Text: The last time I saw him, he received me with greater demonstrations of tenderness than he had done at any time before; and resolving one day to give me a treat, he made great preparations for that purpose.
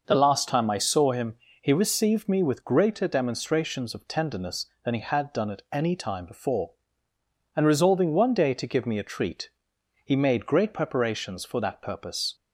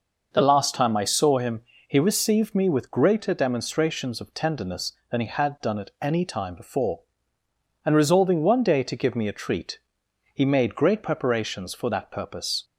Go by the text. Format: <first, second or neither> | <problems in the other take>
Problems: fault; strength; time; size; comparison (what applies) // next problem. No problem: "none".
neither | none